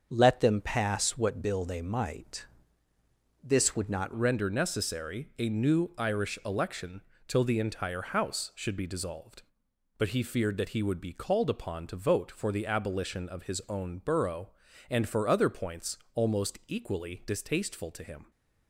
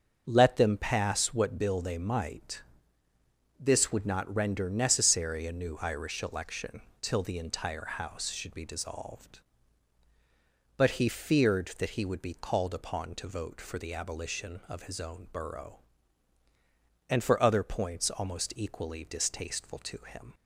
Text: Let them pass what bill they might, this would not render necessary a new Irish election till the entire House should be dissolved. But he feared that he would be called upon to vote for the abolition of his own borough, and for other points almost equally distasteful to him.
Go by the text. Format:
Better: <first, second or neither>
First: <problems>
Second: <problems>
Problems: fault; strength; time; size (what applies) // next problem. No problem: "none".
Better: second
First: starts louder than the rest; until 1.1 s; 7 dB // changes voice at "render"; from 4.1 s on; 14.2 s long // pauses between "election" and "till"; slight; at 7.0 s; 0.24 s long // pauses between "points" and "almost"; slight; at 15.9 s; 0.16 s long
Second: starts louder than the rest; until 1.2 s; 6.5 dB // pauses between "election" and "till"; slight; at 6.8 s; 0.20 s long